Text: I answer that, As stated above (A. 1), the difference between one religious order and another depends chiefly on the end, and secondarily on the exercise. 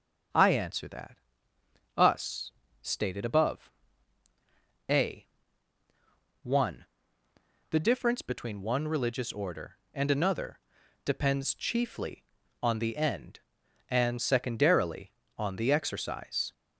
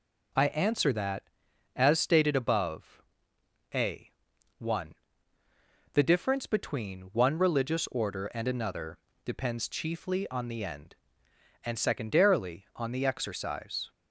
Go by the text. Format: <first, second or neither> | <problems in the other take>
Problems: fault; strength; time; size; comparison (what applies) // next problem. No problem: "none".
second | starts louder than the rest; until 2.1 s; 7 dB // says "Us" for "As"; at 1.9 s // pauses between "another" and "depends"; at 10.6 s; 0.44 s long; slight in the second